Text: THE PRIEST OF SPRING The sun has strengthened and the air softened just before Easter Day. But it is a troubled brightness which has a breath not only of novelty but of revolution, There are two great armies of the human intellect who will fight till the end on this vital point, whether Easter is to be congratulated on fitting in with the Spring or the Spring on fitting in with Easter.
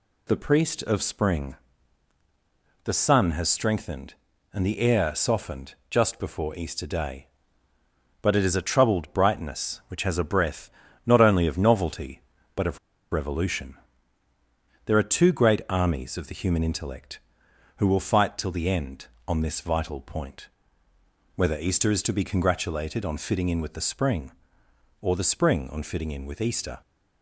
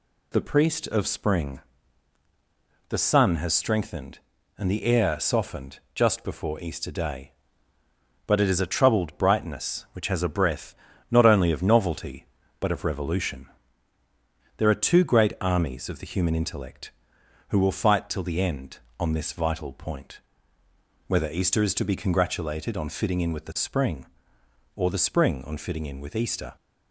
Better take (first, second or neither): second